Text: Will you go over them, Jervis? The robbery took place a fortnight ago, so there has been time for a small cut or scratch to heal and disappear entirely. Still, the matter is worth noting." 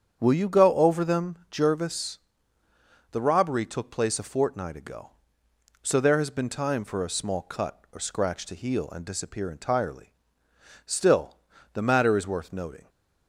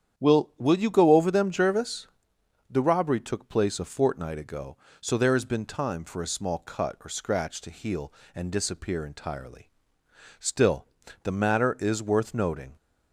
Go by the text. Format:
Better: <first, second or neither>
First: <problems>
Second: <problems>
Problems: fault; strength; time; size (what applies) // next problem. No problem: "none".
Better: first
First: starts louder than the rest; strong; until 1.2 s; 8 dB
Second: starts louder than the rest; strong; until 1.2 s; 9 dB // says "Will" twice; at 0.5 s